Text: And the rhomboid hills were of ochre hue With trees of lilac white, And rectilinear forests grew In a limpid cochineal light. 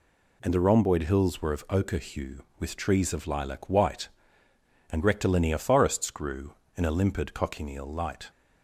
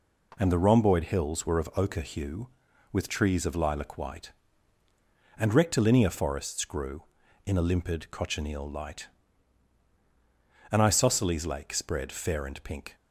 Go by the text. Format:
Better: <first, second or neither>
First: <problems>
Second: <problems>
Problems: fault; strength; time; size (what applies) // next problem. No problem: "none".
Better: first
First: none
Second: goes on to say "An isosceles lake spread fair and pink"; strong; from 10.7 s on; 2.2 s long